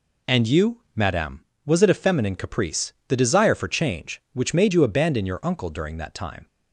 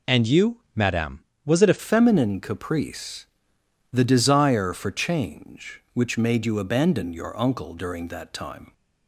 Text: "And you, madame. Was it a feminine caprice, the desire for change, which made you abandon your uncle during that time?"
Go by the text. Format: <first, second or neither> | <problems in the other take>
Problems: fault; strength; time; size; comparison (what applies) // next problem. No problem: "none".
first | changes voice at "feminine"; from 1.7 s on; 7.0 s long